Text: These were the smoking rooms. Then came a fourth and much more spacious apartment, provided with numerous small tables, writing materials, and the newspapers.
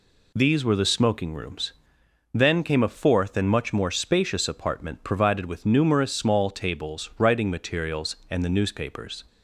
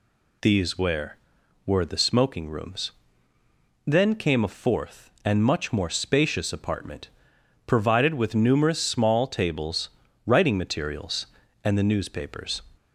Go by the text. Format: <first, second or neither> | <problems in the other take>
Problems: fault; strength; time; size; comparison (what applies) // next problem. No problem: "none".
first | says "were" twice; at 1.6 s